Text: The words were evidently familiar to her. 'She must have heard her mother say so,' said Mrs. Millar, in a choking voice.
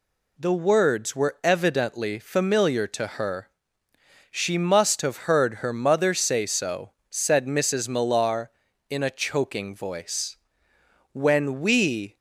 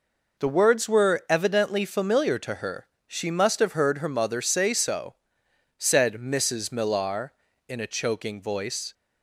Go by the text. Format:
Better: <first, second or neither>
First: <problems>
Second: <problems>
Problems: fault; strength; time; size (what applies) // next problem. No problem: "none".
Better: second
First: goes on to say "When we"; noticeable; from 11.1 s on; 1.0 s long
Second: none